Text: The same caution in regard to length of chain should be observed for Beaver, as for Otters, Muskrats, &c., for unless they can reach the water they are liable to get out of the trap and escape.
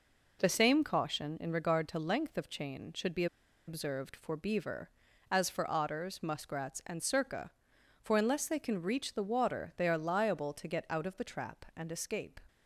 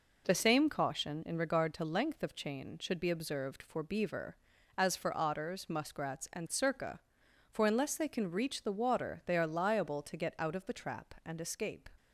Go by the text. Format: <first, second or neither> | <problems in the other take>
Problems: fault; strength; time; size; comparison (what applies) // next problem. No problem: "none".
second | pauses between "be" and "observed"; at 3.2 s; 0.41 s long